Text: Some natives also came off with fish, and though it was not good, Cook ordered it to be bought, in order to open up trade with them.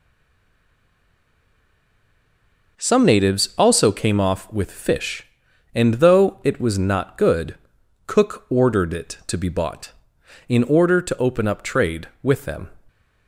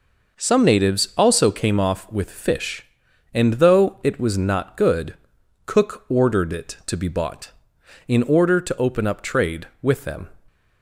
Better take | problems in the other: second | stays silent before the first word; strong; until 2.7 s; 2.7 s long

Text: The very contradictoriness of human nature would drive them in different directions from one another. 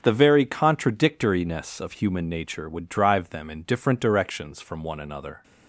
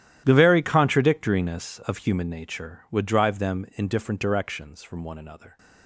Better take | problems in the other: first | gets quieter; strong; throughout; 18.5 dB

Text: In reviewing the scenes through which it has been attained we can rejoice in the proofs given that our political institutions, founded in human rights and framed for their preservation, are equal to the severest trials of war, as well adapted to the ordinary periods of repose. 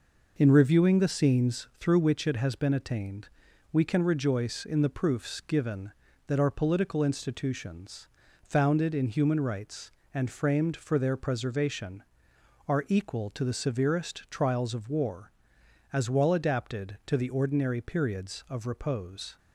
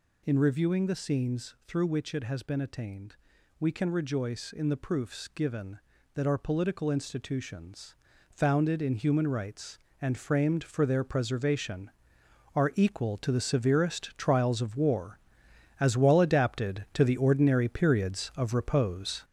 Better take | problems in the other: first | gets louder; noticeable; throughout; 5.5 dB // pauses between "attained" and "we"; at 3.1 s; 0.44 s long; also in the first

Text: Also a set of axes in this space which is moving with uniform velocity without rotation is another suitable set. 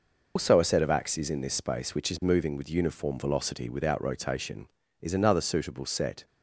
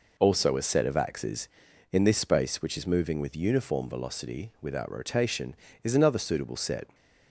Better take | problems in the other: second | loses the start of "Also"; at 0.3 s; 145 ms

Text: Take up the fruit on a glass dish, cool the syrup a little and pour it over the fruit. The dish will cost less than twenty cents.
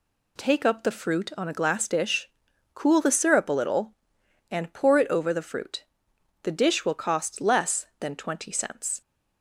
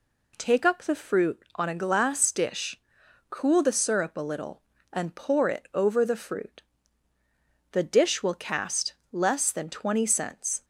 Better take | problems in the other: first | says "cast" for "cost"; at 8.3 s

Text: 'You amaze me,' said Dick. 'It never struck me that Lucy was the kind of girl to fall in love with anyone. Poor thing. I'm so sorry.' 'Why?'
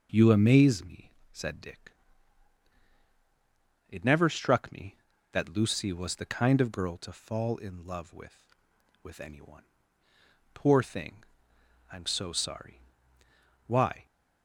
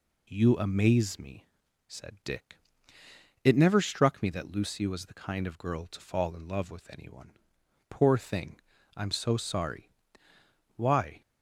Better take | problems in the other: second | says "with" twice; at 9.0 s

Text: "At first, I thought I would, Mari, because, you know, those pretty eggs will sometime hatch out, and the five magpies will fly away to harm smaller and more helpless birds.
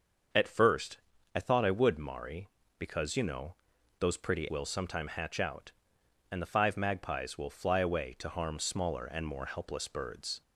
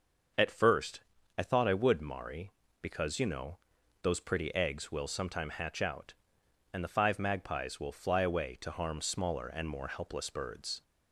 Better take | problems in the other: second | starts louder than the rest; until 1.6 s; 6.5 dB; also in the second // skips "eggs"; at 4.4 s

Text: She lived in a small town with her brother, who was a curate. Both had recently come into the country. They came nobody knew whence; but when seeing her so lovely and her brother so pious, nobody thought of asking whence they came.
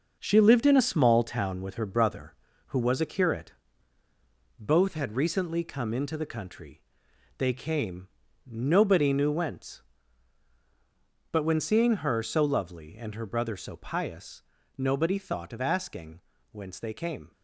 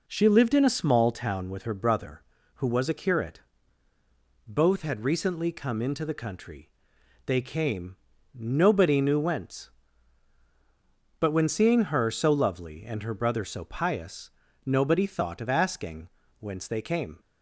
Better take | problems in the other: second | gets quieter; strong; throughout; 7.5 dB // pauses between "came" and "nobody"; at 8.0 s; 0.42 s long; also in the second // pauses between "asking" and "whence"; slight; at 16.1 s; 0.32 s long; slight in the second

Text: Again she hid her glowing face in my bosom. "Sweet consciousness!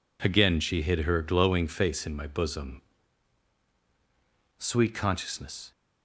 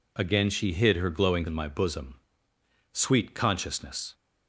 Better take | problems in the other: first | skips "face"; at 1.4 s

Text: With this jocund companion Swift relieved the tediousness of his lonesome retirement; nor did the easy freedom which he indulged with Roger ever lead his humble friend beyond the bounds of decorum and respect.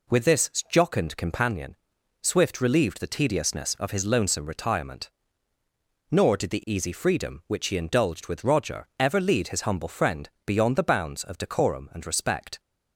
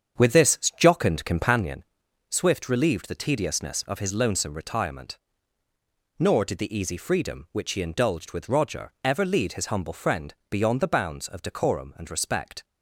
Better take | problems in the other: first | starts louder than the rest; strong; until 2.0 s; 7.5 dB // pauses between "this" and "jocund"; slight; at 0.5 s; 0.22 s long; slight in the first // pauses between "companion" and "Swift"; noticeable; at 1.8 s; 0.48 s long; noticeable in the first // pauses between "friend" and "beyond"; slight; at 10.3 s; 0.16 s long; slight in the first

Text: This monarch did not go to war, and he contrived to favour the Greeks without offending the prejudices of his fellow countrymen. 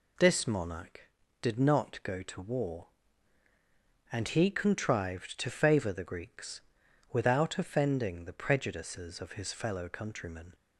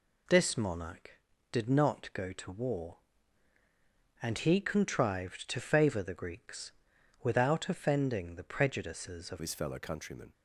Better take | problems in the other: first | pauses between "Greeks" and "without"; noticeable; at 6.7 s; 0.50 s long; noticeable in the first // changes voice at "his"; from 9.4 s on; 0.9 s long

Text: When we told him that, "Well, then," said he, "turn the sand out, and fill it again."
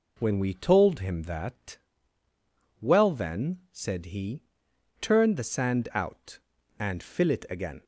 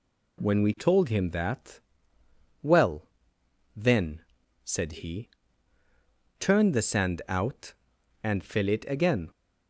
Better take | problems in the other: neither | none

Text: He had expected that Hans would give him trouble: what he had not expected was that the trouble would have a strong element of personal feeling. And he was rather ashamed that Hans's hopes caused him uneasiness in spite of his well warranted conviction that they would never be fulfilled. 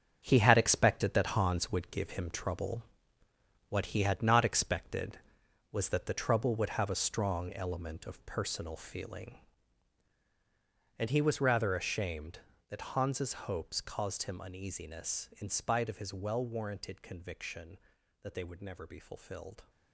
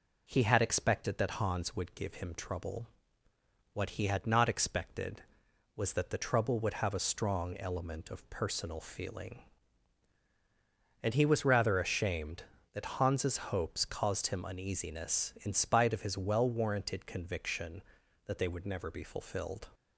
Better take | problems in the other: second | gets quieter; strong; throughout; 10.5 dB // pauses between "Hans's" and "hopes"; slight; at 13.3 s; 0.18 s long; slight in the second

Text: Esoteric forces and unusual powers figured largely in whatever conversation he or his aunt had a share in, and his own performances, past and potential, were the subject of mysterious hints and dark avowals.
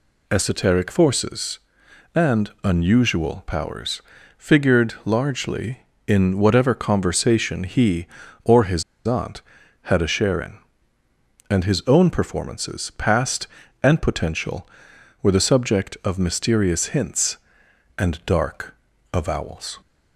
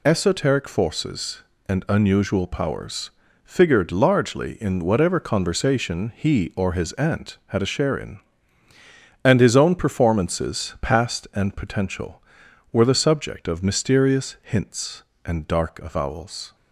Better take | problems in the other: second | pauses between "powers" and "figured"; slight; at 4.0 s; 0.34 s long; slight in the second // pauses between "his" and "aunt"; slight; at 8.8 s; 0.23 s long // pauses between "dark" and "avowals"; at 18.7 s; 0.38 s long

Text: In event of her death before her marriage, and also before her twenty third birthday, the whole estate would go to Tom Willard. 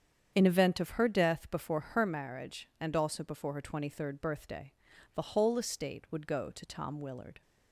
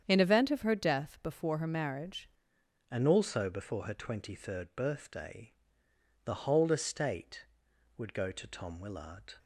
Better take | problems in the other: first | starts louder than the rest; strong; until 1.0 s; 8 dB; strong in the first // changes voice at "and"; from 2.8 s on; 6.5 s long

